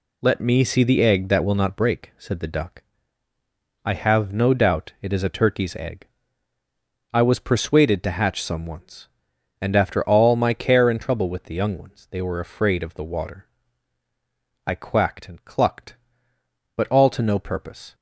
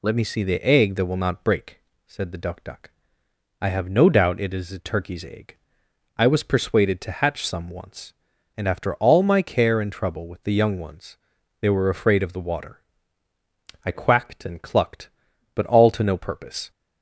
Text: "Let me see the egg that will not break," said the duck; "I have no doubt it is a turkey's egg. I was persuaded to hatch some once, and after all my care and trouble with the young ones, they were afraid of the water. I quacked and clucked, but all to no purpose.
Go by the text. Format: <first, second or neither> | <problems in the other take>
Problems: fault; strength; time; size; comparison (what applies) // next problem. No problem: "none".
first | says "duck" twice; at 2.6 s